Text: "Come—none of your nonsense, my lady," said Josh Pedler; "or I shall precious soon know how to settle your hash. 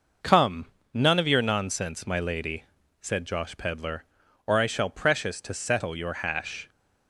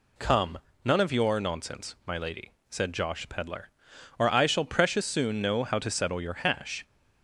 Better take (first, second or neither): second